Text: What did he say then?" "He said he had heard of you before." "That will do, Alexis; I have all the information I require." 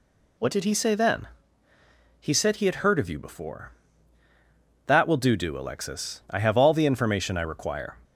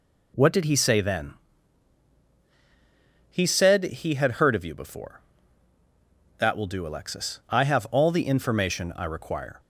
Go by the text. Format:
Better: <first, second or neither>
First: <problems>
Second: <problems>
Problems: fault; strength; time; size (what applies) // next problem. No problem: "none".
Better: second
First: says "do" twice; at 5.3 s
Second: none